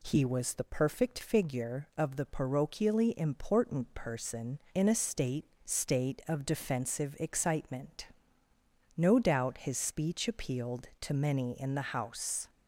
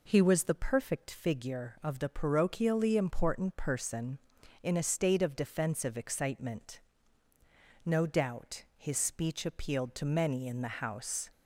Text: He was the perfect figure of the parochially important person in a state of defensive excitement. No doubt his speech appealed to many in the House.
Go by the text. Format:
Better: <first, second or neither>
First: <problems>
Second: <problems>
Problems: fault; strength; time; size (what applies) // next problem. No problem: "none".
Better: second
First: says "state" twice; at 5.6 s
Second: none